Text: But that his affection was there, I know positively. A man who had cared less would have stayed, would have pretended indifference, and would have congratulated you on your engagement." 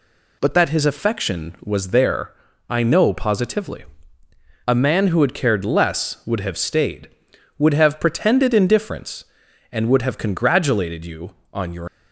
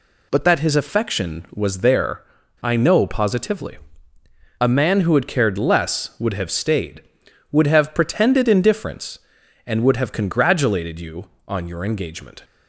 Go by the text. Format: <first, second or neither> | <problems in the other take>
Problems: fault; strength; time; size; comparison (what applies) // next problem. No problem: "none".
second | stops before "engagement"; at 11.8 s